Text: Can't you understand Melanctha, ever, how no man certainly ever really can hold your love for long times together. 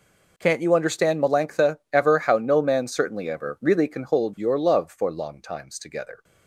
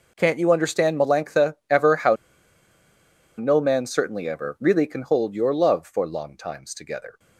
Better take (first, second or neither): first